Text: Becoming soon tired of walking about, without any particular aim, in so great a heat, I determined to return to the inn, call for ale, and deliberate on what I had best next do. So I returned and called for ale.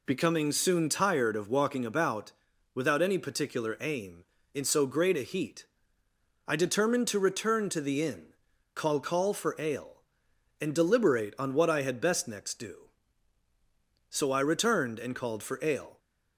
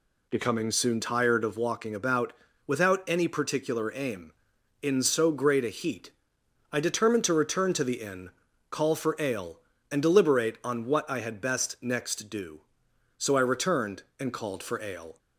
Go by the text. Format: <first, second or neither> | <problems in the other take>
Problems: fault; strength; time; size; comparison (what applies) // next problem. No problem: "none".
second | says "call" twice; at 9.0 s